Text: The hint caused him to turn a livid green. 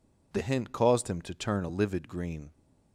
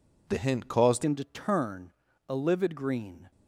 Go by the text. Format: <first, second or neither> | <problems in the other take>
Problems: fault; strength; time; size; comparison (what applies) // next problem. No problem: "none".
first | changes voice at "him"; from 1.0 s on; 2.3 s long // pauses between "turn" and "a"; slight; at 1.9 s; 0.36 s long